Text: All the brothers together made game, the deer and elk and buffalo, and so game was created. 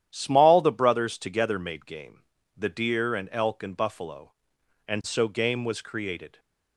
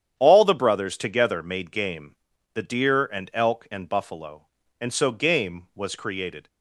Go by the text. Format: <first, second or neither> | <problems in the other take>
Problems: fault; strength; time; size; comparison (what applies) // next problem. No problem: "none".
second | starts louder than the rest; strong; until 1.1 s; 11 dB; strong in the second // says "Small" for "All"; at 0.1 s